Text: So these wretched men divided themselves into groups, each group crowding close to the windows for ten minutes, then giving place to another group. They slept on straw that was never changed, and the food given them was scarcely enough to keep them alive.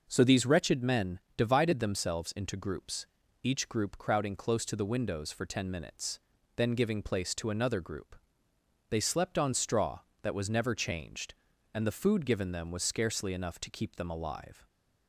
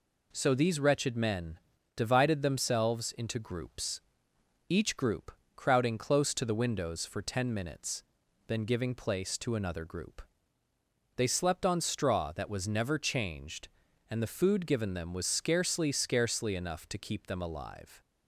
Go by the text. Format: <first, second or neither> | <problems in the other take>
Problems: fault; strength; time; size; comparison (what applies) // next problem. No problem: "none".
first | pauses between "men" and "divided"; at 1.5 s; 0.38 s long; slight in the first // pauses between "group" and "crowding"; slight; at 5.3 s; 0.24 s long // says "scarcely" twice; at 15.9 s